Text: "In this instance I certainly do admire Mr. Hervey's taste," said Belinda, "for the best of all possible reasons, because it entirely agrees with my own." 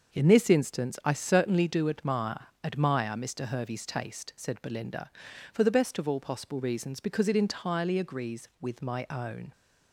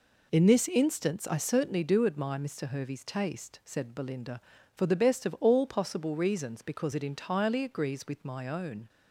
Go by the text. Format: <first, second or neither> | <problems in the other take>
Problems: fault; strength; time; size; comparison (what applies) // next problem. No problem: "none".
second | starts louder than the rest; until 1.1 s; 6.5 dB // says "admire" twice; at 2.6 s